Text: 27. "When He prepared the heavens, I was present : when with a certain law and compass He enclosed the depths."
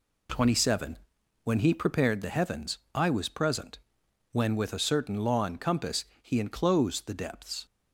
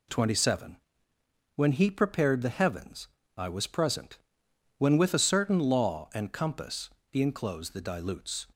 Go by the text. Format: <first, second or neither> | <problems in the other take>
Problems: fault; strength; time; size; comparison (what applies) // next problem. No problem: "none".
first | pauses between "compass" and "He"; slight; at 6.8 s; 0.22 s long; slight in the first // says "dilutes" for "depths"; at 7.8 s